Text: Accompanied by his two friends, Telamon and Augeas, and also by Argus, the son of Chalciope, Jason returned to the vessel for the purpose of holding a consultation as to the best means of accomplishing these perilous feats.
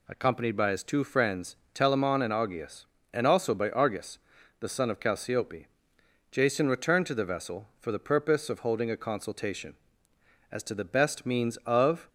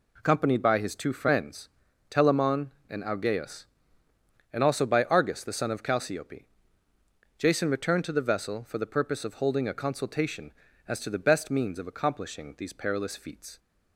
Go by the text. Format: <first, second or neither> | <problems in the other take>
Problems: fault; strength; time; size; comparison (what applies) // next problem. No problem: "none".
second | stops before "accomplishing these perilous feats"; at 12.0 s